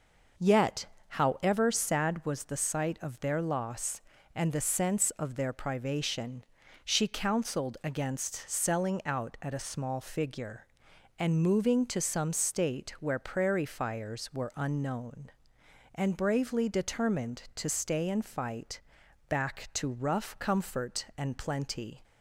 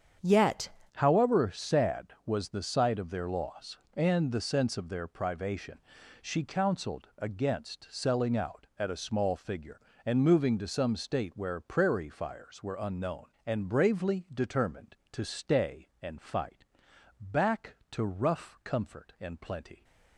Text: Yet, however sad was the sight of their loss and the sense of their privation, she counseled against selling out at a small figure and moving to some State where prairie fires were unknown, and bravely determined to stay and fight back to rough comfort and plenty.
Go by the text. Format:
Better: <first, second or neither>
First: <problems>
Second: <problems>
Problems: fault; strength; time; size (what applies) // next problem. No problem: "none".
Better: first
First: pauses between "fight" and "back"; noticeable; at 18.8 s; 0.48 s long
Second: starts louder than the rest; strong; until 1.4 s; 8 dB // changes voice at "however"; from 0.9 s on; 18.9 s long // pauses between "fight" and "back"; noticeable; at 16.6 s; 0.56 s long